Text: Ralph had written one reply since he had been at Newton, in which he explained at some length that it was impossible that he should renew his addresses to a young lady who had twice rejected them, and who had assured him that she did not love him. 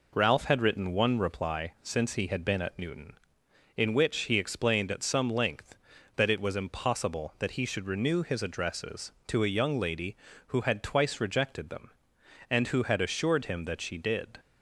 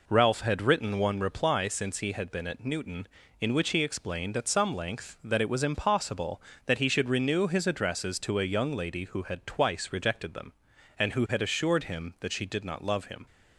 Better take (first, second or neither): second